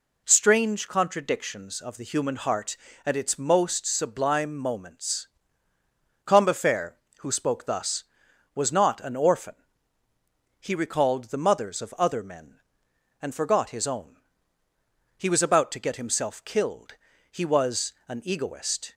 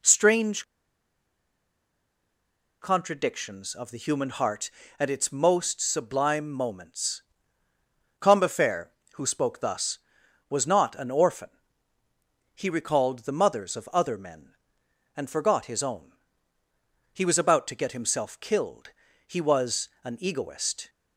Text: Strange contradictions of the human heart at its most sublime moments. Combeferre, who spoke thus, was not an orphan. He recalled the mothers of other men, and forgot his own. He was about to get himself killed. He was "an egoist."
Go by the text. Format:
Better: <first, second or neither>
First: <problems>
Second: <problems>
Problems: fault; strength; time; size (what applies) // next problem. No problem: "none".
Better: first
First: none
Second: pauses between "Strange" and "contradictions"; strong; at 0.6 s; 2.1 s long